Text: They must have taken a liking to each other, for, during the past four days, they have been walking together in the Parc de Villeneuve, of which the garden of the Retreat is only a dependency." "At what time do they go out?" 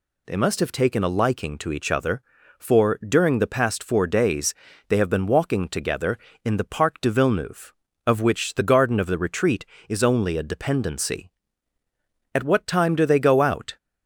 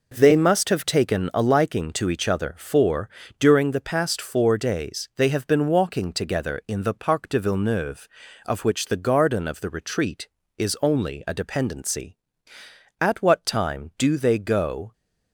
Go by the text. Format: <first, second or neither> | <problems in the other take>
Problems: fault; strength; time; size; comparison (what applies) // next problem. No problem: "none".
first | stops before "out"; at 14.9 s